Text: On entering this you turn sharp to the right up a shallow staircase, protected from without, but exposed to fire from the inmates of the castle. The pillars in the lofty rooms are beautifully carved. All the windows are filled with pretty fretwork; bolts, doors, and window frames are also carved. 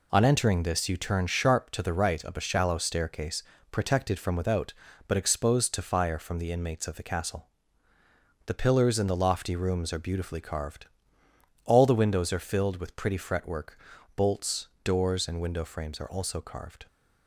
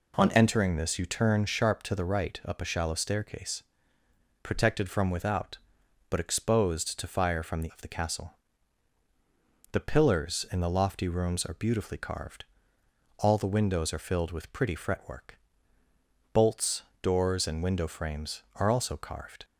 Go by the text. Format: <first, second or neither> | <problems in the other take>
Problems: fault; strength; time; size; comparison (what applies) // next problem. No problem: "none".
first | skips "inmates"; at 7.6 s